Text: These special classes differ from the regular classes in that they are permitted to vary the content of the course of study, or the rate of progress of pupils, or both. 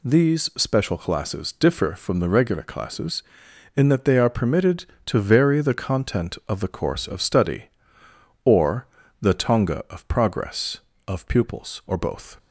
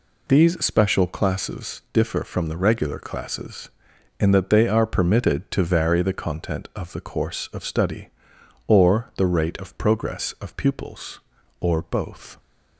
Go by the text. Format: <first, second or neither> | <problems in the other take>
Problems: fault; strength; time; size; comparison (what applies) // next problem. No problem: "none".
second | pauses between "or" and "the"; slight; at 8.8 s; 0.34 s long // says "tonga" for "rate"; at 9.3 s